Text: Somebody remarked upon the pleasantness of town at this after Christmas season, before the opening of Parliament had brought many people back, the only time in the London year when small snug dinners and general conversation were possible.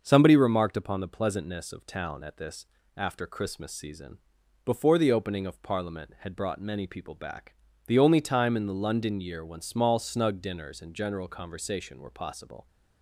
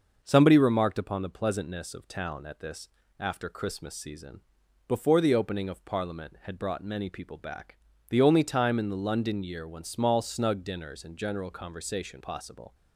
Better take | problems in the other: first | starts louder than the rest; noticeable; until 1.2 s; 6 dB; noticeable in the first // pauses between "this" and "after"; slight; at 2.8 s; 0.30 s long; slight in the first // skips "were"; at 12.2 s

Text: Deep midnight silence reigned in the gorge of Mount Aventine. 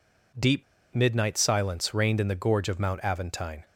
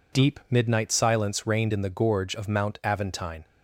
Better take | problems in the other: second | pauses between "Deep" and "midnight"; slight; at 0.6 s; 0.29 s long

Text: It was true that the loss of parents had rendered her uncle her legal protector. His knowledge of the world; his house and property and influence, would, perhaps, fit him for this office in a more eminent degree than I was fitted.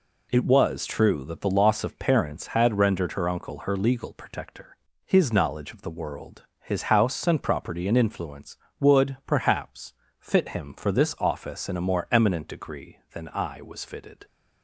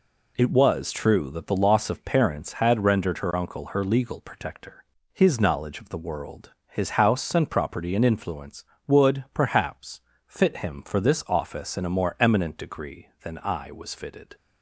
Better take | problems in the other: neither | none

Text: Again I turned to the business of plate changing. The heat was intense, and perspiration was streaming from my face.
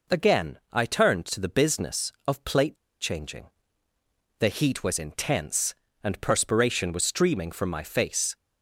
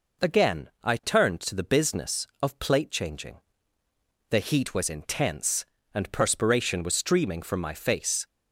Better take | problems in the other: second | pauses between "plate" and "changing"; slight; at 2.7 s; 0.25 s long

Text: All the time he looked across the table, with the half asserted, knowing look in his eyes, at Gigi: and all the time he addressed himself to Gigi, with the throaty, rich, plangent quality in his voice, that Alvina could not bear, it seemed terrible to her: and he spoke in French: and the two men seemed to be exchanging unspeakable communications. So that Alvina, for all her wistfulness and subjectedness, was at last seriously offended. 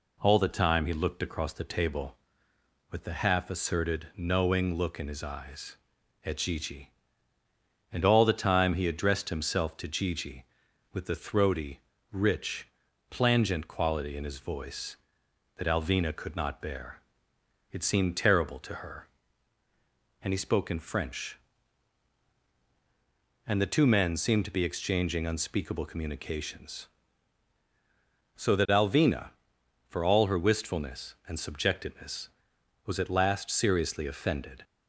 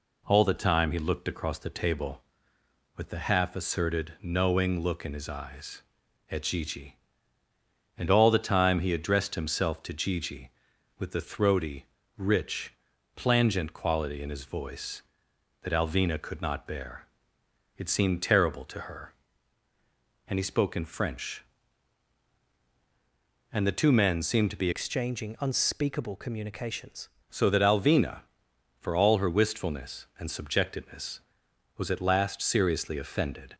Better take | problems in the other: first | changes voice from "exchanging" to "communications"; from 24.7 to 27.0 s; 2.3 s long

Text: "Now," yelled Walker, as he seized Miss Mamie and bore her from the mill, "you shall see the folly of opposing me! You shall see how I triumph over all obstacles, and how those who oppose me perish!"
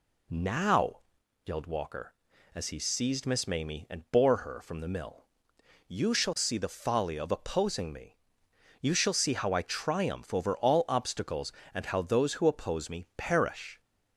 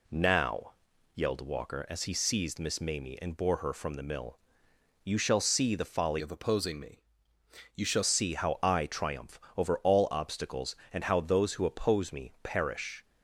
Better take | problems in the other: first | changes voice from "of" to "shall"; from 6.1 to 8.0 s; 1.9 s long // pauses between "triumph" and "over"; slight; at 9.3 s; 0.16 s long

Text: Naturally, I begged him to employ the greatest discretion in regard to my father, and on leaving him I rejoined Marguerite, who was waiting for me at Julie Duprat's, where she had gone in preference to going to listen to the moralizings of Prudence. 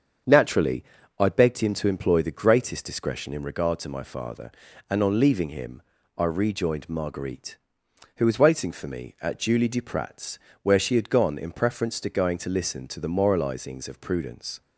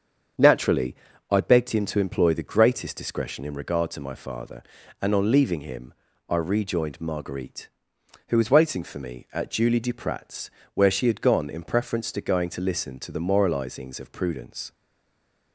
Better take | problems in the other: first | starts louder than the rest; strong; until 1.7 s; 7 dB; strong in the first // pauses between "him" and "I"; slight; at 5.9 s; 0.34 s long; slight in the first // stays silent after the last word; slight; from 14.7 s on; 0.8 s long

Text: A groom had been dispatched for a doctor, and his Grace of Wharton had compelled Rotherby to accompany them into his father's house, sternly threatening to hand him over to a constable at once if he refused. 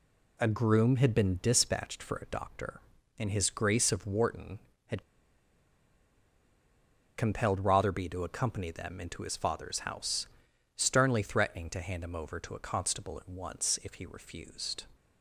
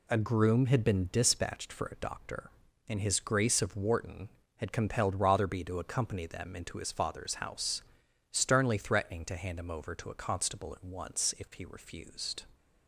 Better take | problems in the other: second | pauses between "had" and "compelled"; strong; at 5.0 s; 2.1 s long

